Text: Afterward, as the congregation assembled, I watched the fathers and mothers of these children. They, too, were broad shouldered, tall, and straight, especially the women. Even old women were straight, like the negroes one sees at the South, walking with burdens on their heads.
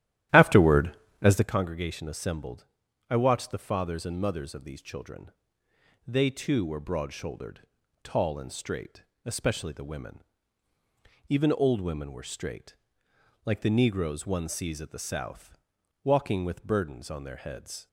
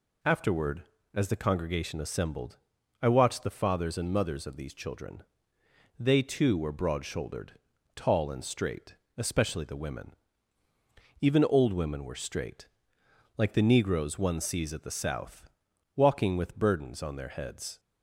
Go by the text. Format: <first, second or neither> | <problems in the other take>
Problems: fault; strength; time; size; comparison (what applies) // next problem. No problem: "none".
second | starts louder than the rest; strong; until 1.6 s; 13 dB